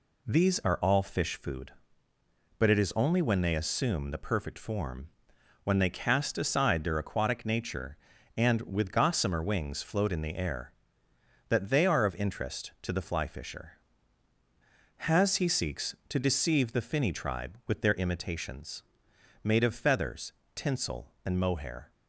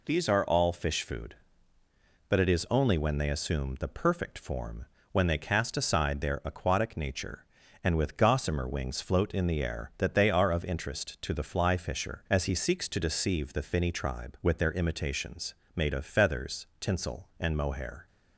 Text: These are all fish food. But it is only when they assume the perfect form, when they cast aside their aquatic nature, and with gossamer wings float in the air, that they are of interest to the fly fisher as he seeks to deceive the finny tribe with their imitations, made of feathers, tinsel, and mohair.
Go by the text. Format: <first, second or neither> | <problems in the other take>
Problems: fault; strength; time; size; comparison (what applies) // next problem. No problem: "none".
second | says "has" for "as"; at 14.9 s